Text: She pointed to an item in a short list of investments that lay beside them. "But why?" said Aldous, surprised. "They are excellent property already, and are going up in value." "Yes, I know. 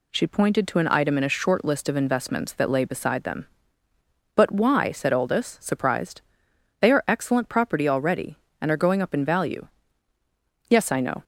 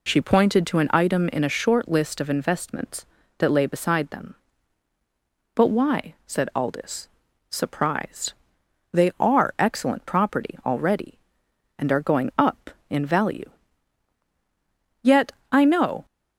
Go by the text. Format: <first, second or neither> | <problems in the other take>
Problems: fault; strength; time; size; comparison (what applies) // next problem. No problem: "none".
first | says "Yet" for "Yes"; at 15.0 s